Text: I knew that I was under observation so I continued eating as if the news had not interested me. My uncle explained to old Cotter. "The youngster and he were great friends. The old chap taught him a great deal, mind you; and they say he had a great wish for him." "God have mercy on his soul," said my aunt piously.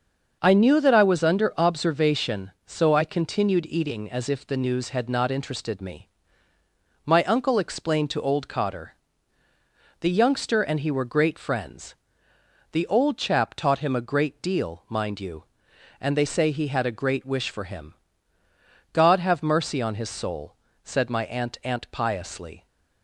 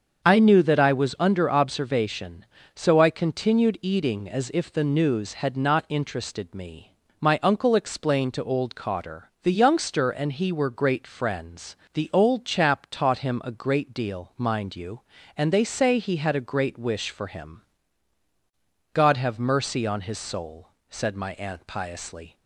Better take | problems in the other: second | starts louder than the rest; until 1.4 s; 6.5 dB; also in the second // says "aunt" twice; at 21.6 s

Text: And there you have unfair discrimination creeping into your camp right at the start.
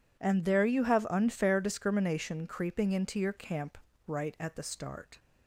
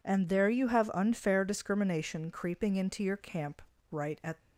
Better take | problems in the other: first | pauses between "camp" and "right"; slight; at 3.6 s; 0.30 s long; slight in the first // stops before "the start"; at 4.3 s

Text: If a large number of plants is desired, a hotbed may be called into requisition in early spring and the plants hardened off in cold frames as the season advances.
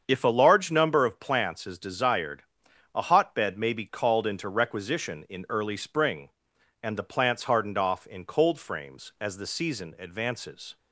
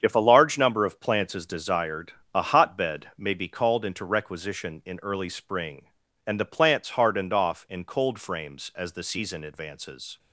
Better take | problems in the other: neither | starts louder than the rest; strong; the same in both

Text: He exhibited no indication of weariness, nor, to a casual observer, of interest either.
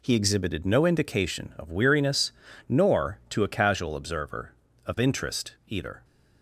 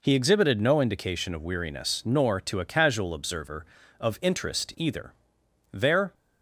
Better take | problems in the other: first | goes on to say "There"; slight; from 5.6 s on; 0.44 s long

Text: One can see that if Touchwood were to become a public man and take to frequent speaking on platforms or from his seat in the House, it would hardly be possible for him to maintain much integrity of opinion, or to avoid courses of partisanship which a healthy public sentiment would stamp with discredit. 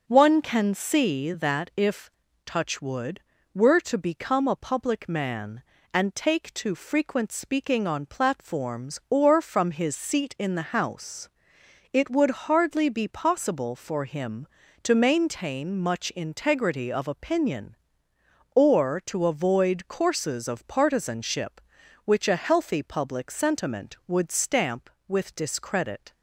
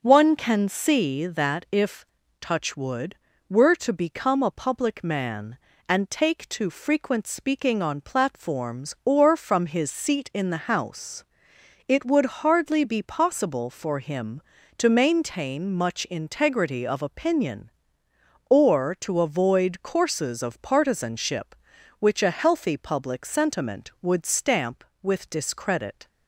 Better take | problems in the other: neither | starts louder than the rest; the same in both // pauses between "if" and "Touchwood"; slight; the same in both

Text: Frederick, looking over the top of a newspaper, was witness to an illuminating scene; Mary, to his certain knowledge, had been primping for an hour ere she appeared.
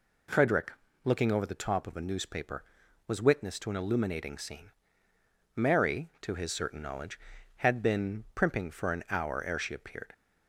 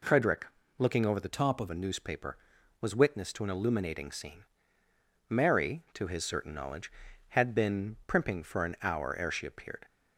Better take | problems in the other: first | changes voice from "top" to "of"; from 1.2 to 1.6 s; 0.4 s long

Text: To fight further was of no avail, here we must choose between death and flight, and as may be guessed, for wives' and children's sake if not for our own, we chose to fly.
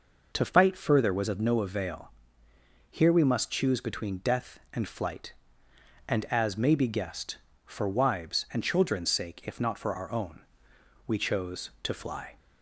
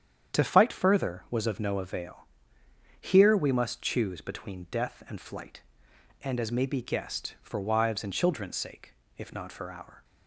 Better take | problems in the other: first | starts louder than the rest; strong; until 1.4 s; 8.5 dB // pauses between "sake" and "if"; slight; at 8.9 s; 0.22 s long // stops before "own we chose to fly"; at 10.0 s

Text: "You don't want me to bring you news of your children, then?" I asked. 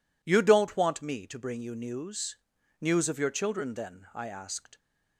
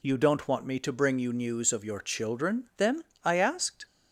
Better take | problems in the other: second | says "news" twice; at 2.7 s

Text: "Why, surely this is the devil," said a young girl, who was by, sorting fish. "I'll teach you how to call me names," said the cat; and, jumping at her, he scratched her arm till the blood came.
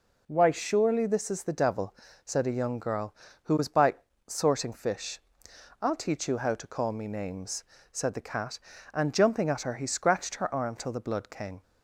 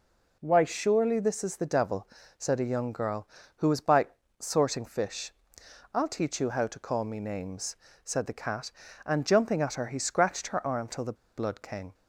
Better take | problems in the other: first | pauses between "the" and "blood"; slight; at 11.1 s; 0.21 s long

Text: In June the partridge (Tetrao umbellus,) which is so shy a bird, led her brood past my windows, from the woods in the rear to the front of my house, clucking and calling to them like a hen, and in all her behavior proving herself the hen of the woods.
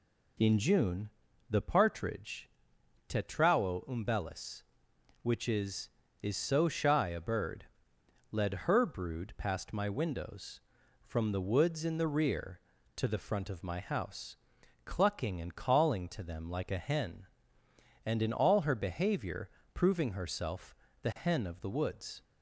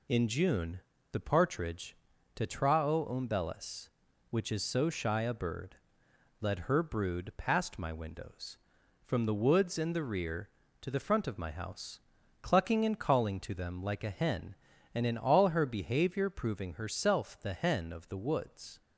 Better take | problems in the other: second | pauses between "June" and "the"; at 1.1 s; 0.40 s long; slight in the second // says "is" twice; at 6.2 s // pauses between "behavior" and "proving"; slight; at 19.5 s; 0.24 s long // pauses between "herself" and "the"; slight; at 20.7 s; 0.26 s long

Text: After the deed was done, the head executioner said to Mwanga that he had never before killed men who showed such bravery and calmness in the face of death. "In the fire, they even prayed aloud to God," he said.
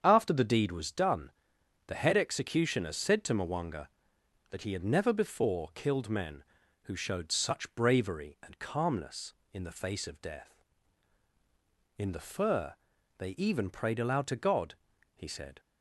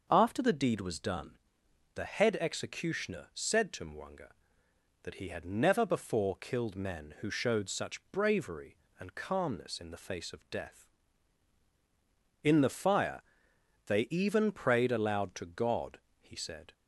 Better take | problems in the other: second | starts louder than the rest; strong; until 1.0 s; 7.5 dB // says "fur" for "fire"; at 12.2 s

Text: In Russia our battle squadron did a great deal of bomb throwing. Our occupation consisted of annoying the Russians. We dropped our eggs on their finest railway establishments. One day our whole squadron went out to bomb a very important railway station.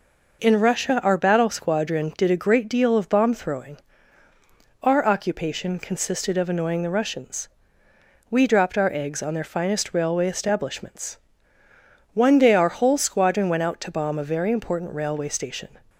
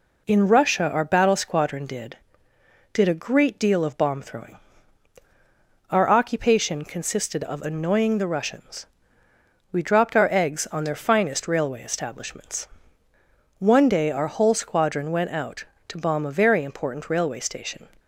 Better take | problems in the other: first | says "did" twice; at 2.9 s

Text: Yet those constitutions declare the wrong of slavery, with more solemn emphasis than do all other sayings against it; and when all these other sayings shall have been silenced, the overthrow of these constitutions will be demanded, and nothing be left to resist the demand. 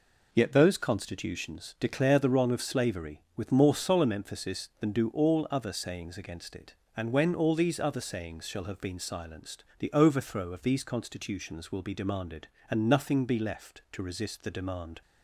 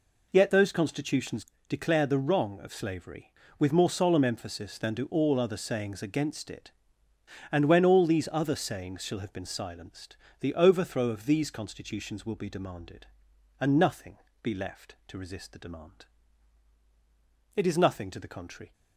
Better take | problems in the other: first | pauses between "constitutions" and "declare"; slight; at 1.4 s; 0.22 s long // pauses between "nothing" and "be"; slight; at 14.1 s; 0.24 s long // goes on to say "It is nothing to the contrary"; noticeable; from 17.5 s on; 1.1 s long

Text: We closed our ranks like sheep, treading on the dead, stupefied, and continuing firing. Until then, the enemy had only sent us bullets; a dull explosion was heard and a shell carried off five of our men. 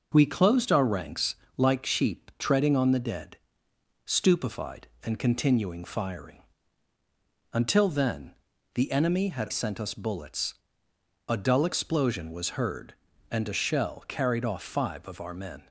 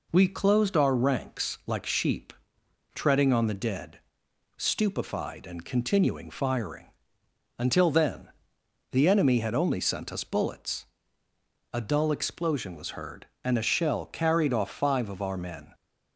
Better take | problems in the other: second | pauses between "ranks" and "like"; slight; at 1.3 s; 0.22 s long // skips "only"; at 9.4 s

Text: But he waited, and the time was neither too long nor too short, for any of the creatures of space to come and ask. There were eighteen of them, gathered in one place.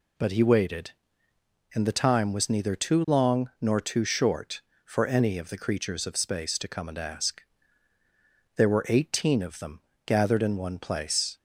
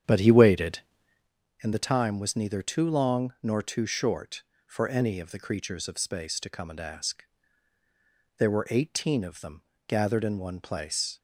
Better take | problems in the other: first | starts louder than the rest; strong; until 1.3 s; 8.5 dB

